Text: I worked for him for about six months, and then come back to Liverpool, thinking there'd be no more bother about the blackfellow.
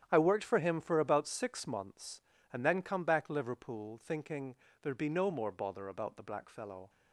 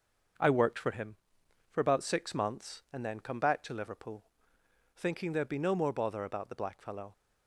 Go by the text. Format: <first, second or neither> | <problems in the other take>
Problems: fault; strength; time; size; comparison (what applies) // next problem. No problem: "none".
second | starts louder than the rest; strong; until 1.1 s; 10 dB; also in the second // skips "to"; at 3.2 s // pauses between "thinking" and "there'd"; slight; at 4.5 s; 0.26 s long